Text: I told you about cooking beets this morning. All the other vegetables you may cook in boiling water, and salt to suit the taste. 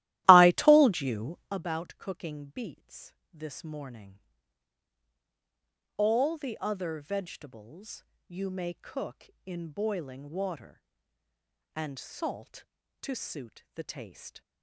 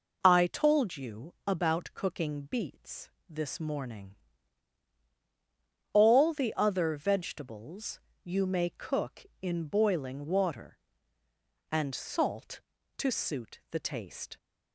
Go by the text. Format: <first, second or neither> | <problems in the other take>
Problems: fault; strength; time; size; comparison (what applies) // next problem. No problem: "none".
second | starts louder than the rest; strong; until 1.5 s; 15.5 dB // pauses between "beets" and "this"; slight; at 3.1 s; 0.18 s long; slight in the second // pauses between "vegetables" and "you"; slight; at 8.0 s; 0.22 s long; slight in the second